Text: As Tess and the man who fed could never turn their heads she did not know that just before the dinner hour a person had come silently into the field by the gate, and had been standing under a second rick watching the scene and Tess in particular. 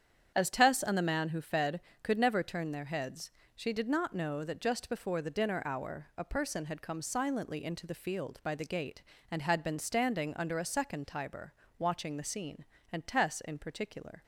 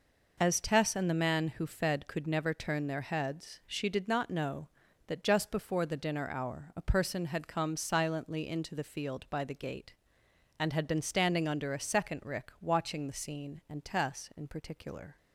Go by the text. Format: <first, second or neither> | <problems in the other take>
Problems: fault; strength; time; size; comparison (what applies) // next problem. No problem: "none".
second | starts louder than the rest; strong; until 1.3 s; 8.5 dB // pauses between "heads" and "she"; slight; at 3.2 s; 0.26 s long // says "tiber" for "rick"; at 11.0 s